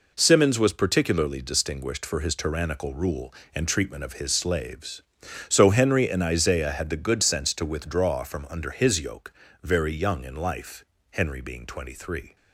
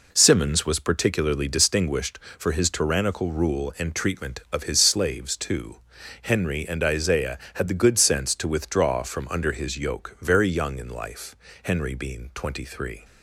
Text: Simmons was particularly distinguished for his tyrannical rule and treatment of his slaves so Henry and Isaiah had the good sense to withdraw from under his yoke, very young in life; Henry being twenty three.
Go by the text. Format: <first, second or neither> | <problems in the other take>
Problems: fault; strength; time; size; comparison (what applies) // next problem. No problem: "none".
first | says "too" for "so"; at 5.3 s